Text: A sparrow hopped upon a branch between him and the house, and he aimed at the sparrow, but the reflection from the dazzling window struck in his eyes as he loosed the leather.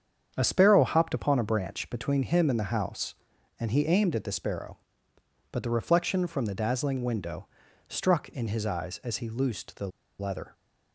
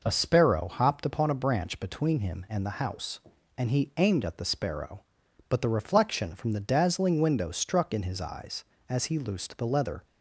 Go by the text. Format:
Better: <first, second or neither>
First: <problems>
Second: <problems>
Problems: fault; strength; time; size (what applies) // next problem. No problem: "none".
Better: second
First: starts louder than the rest; strong; until 1.3 s; 8 dB // pauses between "window" and "struck"; at 7.4 s; 0.42 s long // pauses between "the" and "leather"; slight; at 9.8 s; 0.30 s long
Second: none